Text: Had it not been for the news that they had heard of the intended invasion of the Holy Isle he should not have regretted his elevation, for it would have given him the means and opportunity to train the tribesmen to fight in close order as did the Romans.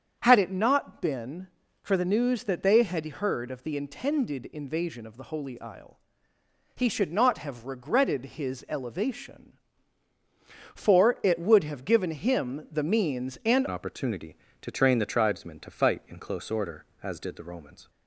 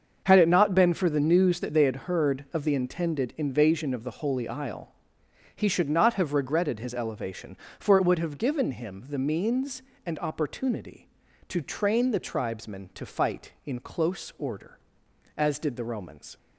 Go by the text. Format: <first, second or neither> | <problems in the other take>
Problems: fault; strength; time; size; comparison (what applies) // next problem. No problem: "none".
second | starts louder than the rest; strong; until 1.2 s; 7.5 dB; also in the second // pauses between "Isle" and "he"; noticeable; at 5.9 s; 0.76 s long; noticeable in the second // changes voice at "opportunity"; from 13.6 s on; 4.2 s long